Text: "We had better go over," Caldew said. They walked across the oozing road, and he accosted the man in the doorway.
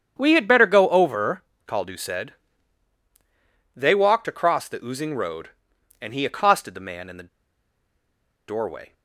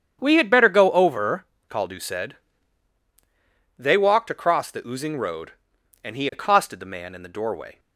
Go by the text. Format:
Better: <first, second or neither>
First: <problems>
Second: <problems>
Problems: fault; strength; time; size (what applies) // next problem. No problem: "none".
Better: second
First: starts louder than the rest; strong; until 1.1 s; 8.5 dB // pauses between "the" and "doorway"; at 7.2 s; 1.2 s long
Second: starts louder than the rest; strong; until 1.2 s; 8.5 dB